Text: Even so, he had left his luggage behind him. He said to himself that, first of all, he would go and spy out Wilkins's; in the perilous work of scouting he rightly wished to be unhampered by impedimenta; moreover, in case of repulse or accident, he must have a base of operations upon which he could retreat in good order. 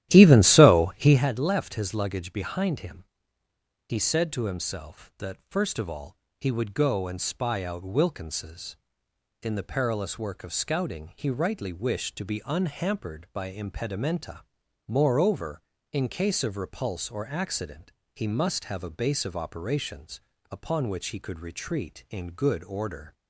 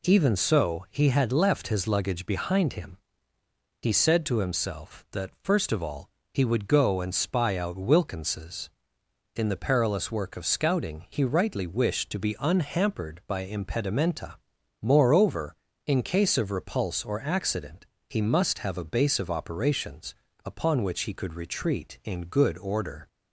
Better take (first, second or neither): second